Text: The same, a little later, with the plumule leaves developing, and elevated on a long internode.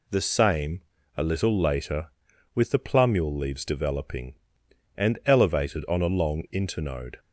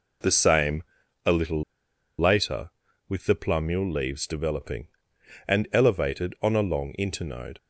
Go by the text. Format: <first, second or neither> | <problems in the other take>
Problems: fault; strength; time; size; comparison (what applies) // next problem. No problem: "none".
first | pauses between "little" and "later"; noticeable; at 1.6 s; 0.55 s long